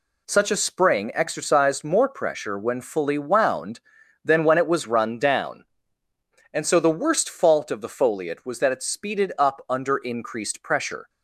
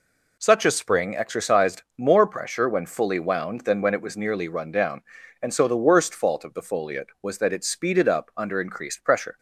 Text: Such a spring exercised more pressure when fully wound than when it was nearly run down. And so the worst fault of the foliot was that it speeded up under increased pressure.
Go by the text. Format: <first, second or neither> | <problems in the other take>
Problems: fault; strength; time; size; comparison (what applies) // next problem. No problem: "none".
second | skips "nearly"; at 4.8 s